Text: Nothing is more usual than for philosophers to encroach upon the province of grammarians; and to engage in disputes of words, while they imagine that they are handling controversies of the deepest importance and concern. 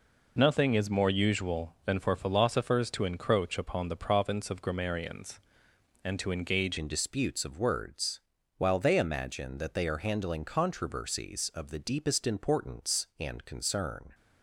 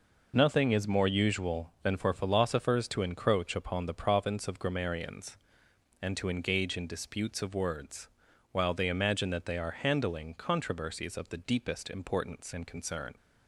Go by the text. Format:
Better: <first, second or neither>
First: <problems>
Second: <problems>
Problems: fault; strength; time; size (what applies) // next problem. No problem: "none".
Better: second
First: changes voice at "in"; from 6.7 s on; 7.4 s long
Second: none